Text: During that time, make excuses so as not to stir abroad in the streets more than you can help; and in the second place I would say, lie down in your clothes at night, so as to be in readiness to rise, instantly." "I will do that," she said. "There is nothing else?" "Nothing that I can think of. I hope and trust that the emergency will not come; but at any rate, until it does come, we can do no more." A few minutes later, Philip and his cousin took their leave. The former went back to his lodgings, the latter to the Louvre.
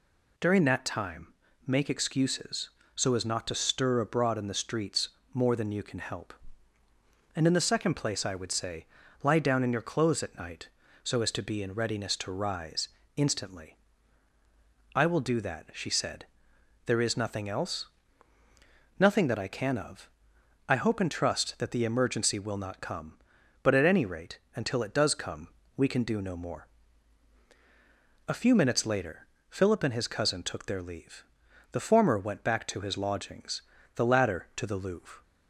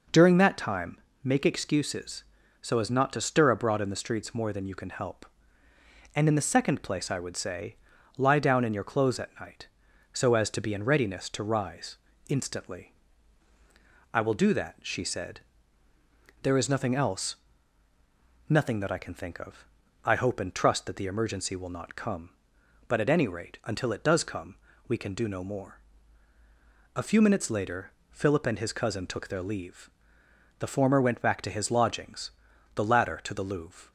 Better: second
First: pauses between "streets" and "more"; slight; at 5.0 s; 0.24 s long // skips "think"; at 19.7 s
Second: none

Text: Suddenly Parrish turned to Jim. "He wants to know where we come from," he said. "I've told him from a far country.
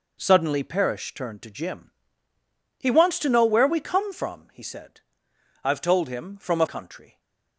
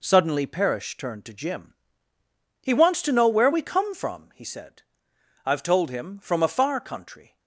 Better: second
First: skips "far"; at 6.6 s // stays silent after the last word; slight; from 7.0 s on; 0.5 s long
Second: none

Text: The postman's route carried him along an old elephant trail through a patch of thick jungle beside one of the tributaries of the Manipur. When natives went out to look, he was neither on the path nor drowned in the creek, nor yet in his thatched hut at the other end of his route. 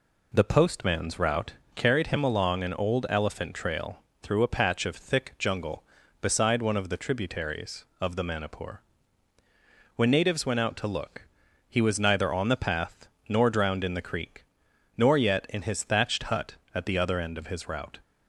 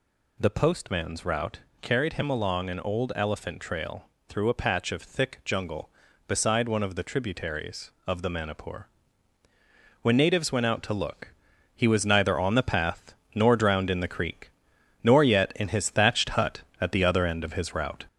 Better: first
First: pauses between "route" and "carried"; slight; at 1.5 s; 0.22 s long // pauses between "trail" and "through"; slight; at 3.9 s; 0.24 s long // pauses between "path" and "nor"; slight; at 13.0 s; 0.20 s long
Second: gets louder; throughout; 4 dB // pauses between "route" and "carried"; slight; at 1.5 s; 0.22 s long // pauses between "trail" and "through"; slight; at 4.0 s; 0.24 s long // pauses between "path" and "nor"; slight; at 13.1 s; 0.20 s long

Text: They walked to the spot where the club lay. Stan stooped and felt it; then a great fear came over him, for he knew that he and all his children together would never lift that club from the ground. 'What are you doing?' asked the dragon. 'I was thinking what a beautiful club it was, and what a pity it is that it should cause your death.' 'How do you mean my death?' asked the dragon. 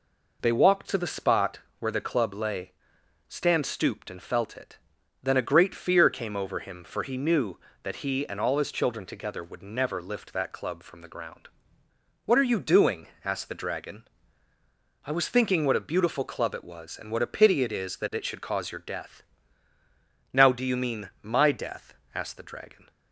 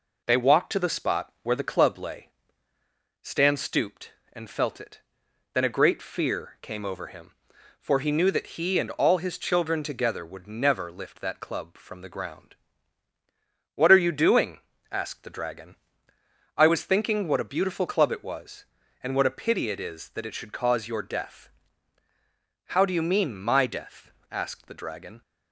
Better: second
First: pauses between "spot" and "where"; slight; at 1.5 s; 0.20 s long // says "Now" for "How"; at 20.3 s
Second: none

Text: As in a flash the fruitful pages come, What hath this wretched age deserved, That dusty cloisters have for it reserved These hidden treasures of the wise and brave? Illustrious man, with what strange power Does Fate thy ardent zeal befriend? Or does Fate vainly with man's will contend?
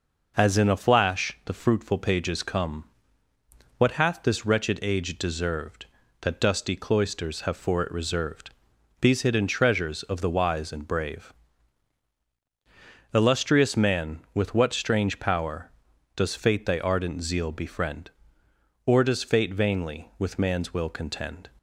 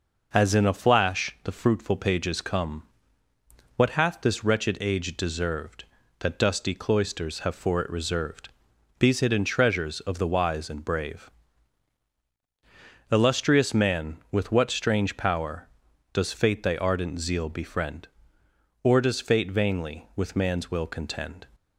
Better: neither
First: pauses between "reserved" and "These"; noticeable; at 8.4 s; 0.52 s long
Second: pauses between "reserved" and "These"; noticeable; at 8.4 s; 0.52 s long

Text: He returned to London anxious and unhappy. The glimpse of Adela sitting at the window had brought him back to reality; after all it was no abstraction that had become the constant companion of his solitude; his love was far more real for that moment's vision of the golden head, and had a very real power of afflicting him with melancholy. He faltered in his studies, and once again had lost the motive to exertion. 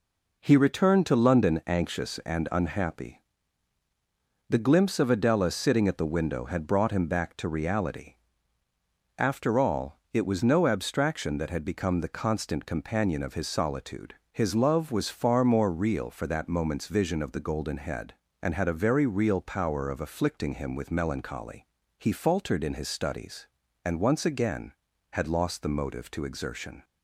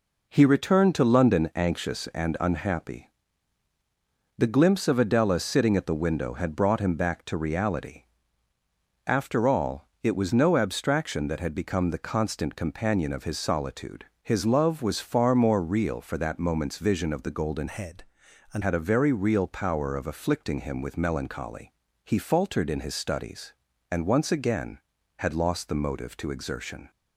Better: first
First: none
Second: pauses between "all" and "it"; slight; at 9.8 s; 0.16 s long // changes voice from "head" to "and"; from 17.6 to 18.6 s; 1.0 s long

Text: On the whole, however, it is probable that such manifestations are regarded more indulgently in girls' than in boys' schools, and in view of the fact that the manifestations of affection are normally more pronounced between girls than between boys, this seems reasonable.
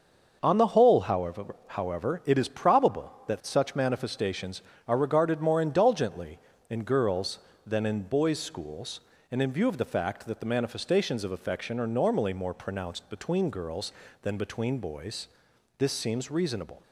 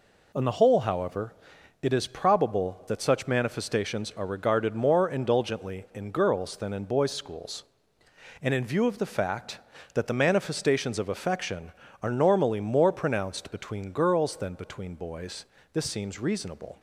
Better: second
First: starts louder than the rest; until 1.4 s; 6.5 dB // says "however" twice; at 1.6 s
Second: none

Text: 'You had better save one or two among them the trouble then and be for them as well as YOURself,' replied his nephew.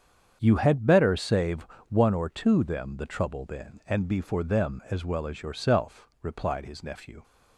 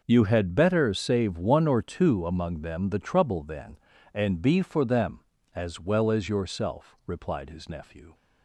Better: second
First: starts louder than the rest; strong; until 1.4 s; 7.5 dB // pauses between "save" and "one"; slight; at 1.6 s; 0.22 s long // skips "among"; at 2.6 s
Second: none

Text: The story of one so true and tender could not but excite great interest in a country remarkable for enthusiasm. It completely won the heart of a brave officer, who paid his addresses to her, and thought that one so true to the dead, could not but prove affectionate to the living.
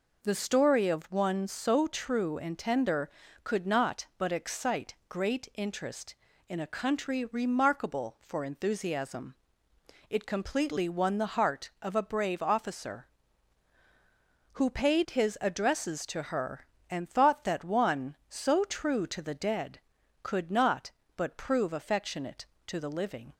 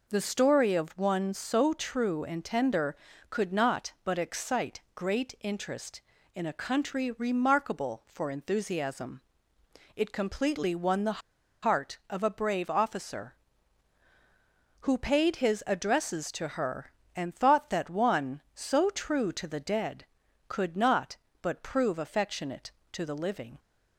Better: first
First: pauses between "excite" and "great"; slight; at 4.9 s; 0.16 s long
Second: pauses between "excite" and "great"; slight; at 4.7 s; 0.16 s long // pauses between "the" and "heart"; at 11.1 s; 0.43 s long

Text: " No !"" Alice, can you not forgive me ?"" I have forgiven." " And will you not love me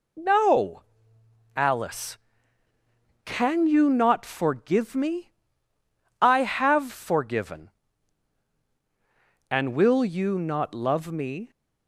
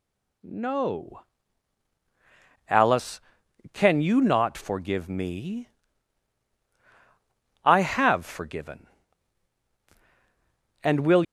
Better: first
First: none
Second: stops before "you not love me"; at 11.2 s

